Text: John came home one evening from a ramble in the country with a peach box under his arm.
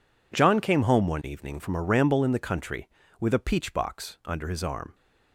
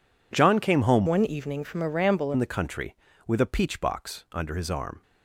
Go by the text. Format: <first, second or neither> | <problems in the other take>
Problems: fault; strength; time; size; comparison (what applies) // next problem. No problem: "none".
first | changes voice from "one" to "ramble"; from 1.0 to 2.3 s; 1.3 s long